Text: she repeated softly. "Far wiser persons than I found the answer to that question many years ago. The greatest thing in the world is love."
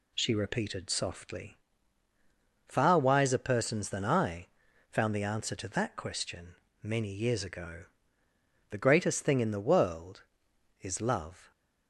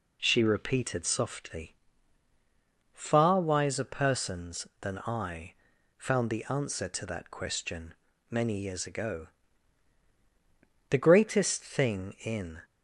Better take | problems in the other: first | pauses between "I" and "found"; at 5.5 s; 0.42 s long; also in the first // pauses between "question" and "many"; slight; at 7.9 s; 0.34 s long; slight in the first // stops before "the world is love"; at 12.6 s

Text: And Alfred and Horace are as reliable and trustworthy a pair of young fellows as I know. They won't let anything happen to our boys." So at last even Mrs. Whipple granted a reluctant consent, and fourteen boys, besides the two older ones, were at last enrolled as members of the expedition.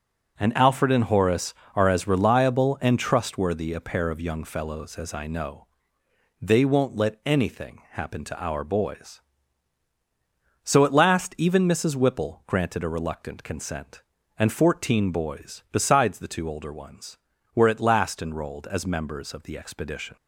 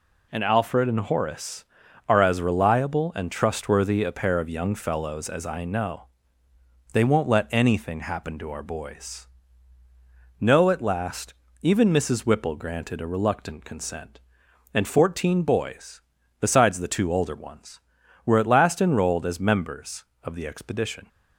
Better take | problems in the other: first | says "No" for "So"; at 10.3 s // pauses between "last" and "even"; slight; at 11.3 s; 0.26 s long

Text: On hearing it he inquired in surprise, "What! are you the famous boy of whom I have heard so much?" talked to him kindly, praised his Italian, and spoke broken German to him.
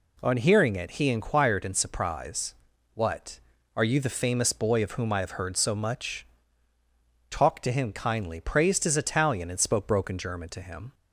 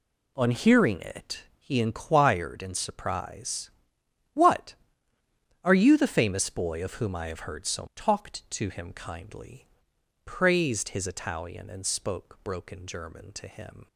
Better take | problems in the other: first | pauses between "it" and "he"; slight; at 1.4 s; 0.16 s long // skips "much"; at 7.9 s

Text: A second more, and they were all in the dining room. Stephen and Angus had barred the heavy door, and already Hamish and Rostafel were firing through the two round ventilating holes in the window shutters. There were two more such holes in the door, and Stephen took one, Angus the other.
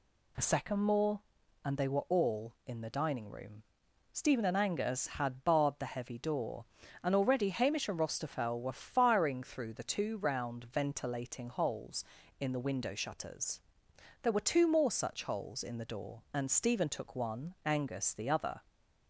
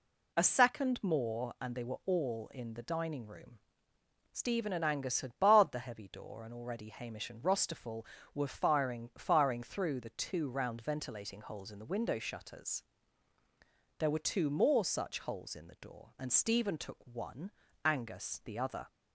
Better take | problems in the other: first | says "firing" twice; at 9.1 s

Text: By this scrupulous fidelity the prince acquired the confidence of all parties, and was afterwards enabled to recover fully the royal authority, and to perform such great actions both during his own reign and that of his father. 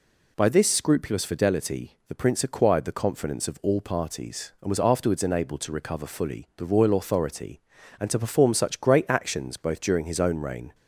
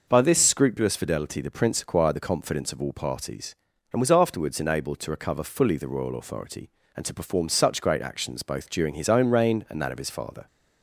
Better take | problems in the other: second | stops before "and that of his father"; at 10.7 s

